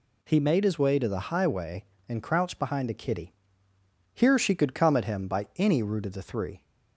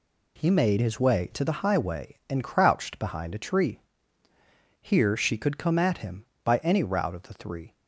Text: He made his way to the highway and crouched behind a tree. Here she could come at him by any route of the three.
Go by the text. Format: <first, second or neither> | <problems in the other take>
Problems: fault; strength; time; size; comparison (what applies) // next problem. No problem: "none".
second | says "kitty" for "tree"; at 2.9 s